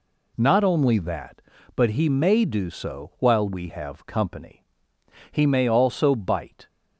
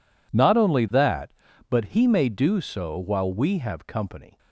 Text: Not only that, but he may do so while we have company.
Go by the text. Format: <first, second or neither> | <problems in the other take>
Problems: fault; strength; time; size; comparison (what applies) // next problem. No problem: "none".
second | goes on to say "He may also bite"; from 5.3 s on; 1.3 s long